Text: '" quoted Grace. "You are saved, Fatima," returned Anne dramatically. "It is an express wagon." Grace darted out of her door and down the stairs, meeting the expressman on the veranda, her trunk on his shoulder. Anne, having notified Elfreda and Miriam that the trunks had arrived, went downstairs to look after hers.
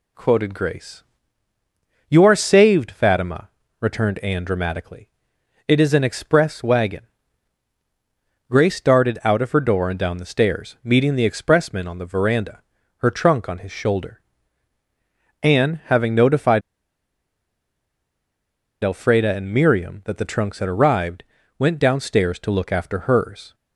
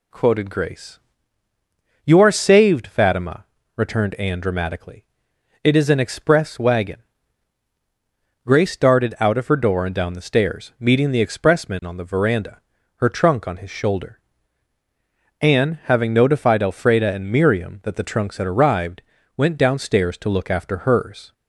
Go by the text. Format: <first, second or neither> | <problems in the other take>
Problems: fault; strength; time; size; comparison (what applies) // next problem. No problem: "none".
second | pauses between "notified" and "Elfreda"; strong; at 16.6 s; 2.2 s long